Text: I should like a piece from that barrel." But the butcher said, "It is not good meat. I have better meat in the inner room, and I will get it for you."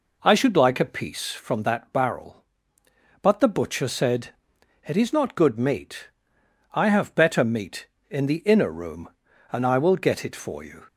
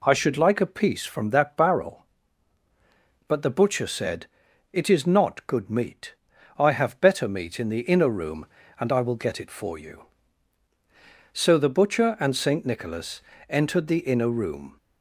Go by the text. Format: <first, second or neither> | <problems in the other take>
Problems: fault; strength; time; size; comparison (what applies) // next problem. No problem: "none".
first | goes on to say "So the butcher and Saint Nicholas entered the inner room"; strong; from 11.3 s on; 3.4 s long